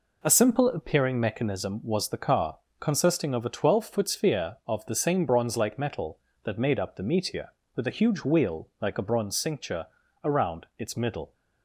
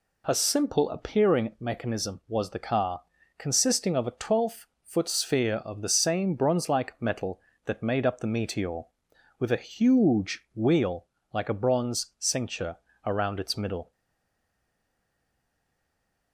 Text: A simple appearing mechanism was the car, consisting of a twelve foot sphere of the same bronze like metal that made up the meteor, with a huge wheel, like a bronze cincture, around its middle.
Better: first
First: none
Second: pauses between "twelve" and "foot"; slight; at 4.6 s; 0.18 s long // stays silent after the last word; from 13.9 s on; 2.4 s long

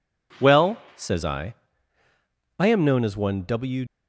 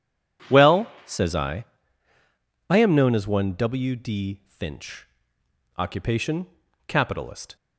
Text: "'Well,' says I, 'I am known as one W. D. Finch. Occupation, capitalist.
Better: second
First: stops before "D Finch Occupation capitalist"; at 3.8 s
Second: none

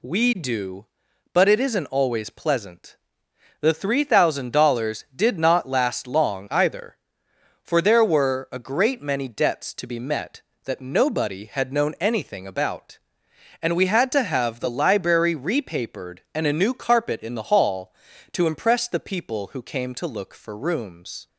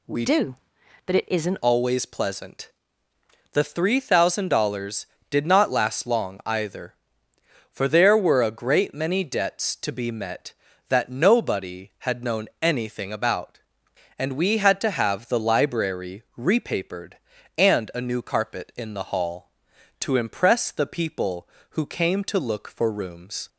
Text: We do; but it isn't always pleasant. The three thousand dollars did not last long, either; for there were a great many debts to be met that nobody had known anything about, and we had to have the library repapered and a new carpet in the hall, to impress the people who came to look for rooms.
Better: first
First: none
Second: changes voice from "do" to "isn't"; from 0.2 to 1.5 s; 1.3 s long // pauses between "known" and "anything"; slight; at 12.4 s; 0.16 s long // pauses between "library" and "repapered"; slight; at 16.2 s; 0.16 s long

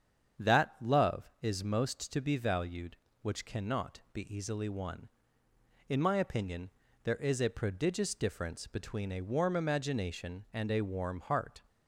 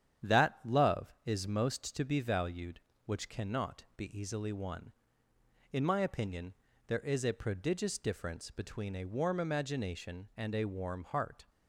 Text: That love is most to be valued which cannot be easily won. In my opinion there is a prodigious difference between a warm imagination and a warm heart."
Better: first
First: starts louder than the rest; strong; until 1.6 s; 8 dB // pauses between "opinion" and "there"; slight; at 6.7 s; 0.34 s long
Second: gets quieter; throughout; 3.5 dB // starts louder than the rest; strong; until 1.4 s; 9 dB // pauses between "opinion" and "there"; slight; at 6.5 s; 0.34 s long

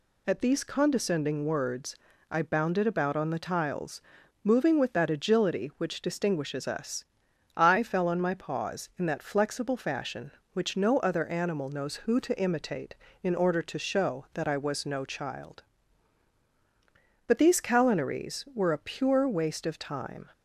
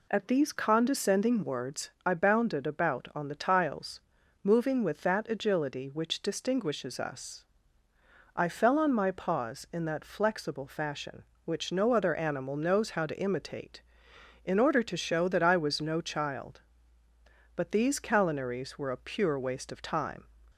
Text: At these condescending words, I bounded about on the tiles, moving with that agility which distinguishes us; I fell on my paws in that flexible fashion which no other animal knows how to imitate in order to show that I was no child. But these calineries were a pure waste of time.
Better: second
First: says "who" for "how"; at 11.9 s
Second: none

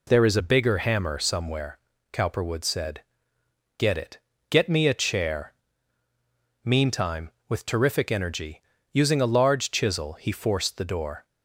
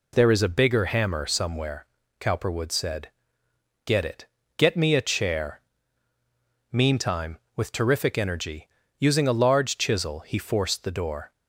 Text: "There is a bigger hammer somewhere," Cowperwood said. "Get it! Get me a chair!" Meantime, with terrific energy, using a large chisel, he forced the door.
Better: neither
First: none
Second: none

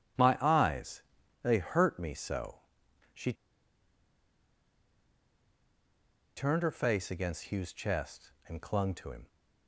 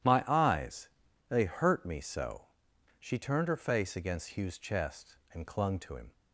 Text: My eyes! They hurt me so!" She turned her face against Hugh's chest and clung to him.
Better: second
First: pauses between "She" and "turned"; strong; at 3.3 s; 3.0 s long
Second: none

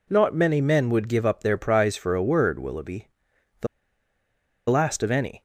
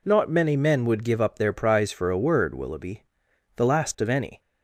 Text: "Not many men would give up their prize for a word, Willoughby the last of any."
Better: second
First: pauses between "Willoughby" and "the"; noticeable; at 3.0 s; 0.52 s long // pauses between "the" and "last"; at 3.6 s; 1.0 s long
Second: pauses between "Willoughby" and "the"; noticeable; at 3.0 s; 0.52 s long

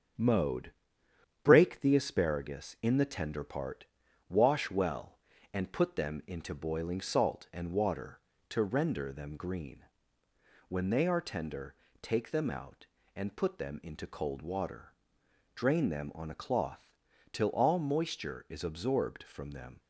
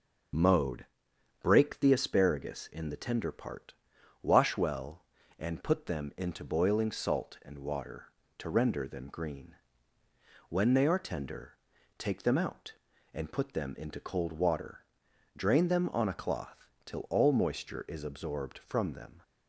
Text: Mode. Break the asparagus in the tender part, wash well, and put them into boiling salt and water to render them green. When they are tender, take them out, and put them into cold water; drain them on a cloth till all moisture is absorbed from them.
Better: second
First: gets quieter; noticeable; throughout; 4.5 dB // starts louder than the rest; strong; until 1.9 s; 7 dB // pauses between "cloth" and "till"; slight; at 16.9 s; 0.36 s long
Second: starts louder than the rest; until 1.9 s; 6.5 dB // pauses between "cloth" and "till"; slight; at 16.6 s; 0.18 s long

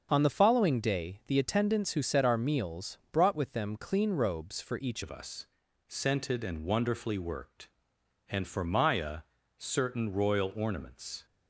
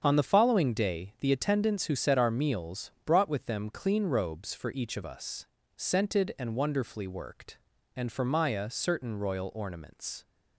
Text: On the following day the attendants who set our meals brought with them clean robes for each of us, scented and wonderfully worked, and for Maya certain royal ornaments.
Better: second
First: starts louder than the rest; until 1.1 s; 6.5 dB // changes voice at "of"; from 5.0 s on; 6.2 s long // pauses between "Maya" and "certain"; at 9.1 s; 0.40 s long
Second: starts louder than the rest; strong; until 1.0 s; 7.5 dB

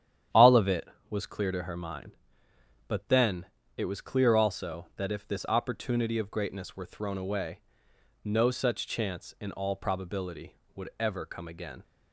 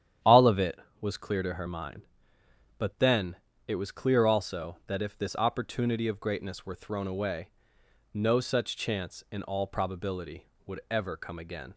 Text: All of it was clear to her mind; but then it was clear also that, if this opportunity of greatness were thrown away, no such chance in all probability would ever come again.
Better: neither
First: starts louder than the rest; strong; until 1.5 s; 10 dB // pauses between "then" and "it"; slight; at 3.4 s; 0.30 s long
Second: starts louder than the rest; strong; until 1.4 s; 10 dB // pauses between "then" and "it"; slight; at 3.3 s; 0.30 s long

